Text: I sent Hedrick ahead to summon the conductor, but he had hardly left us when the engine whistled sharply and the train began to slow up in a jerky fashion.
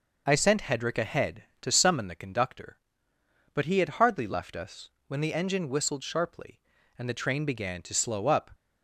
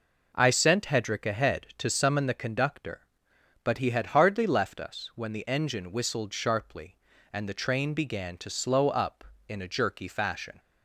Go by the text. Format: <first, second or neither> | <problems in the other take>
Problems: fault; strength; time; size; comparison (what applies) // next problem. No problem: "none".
second | pauses between "us" and "when"; slight; at 4.8 s; 0.18 s long // stops before "in a jerky fashion"; at 8.5 s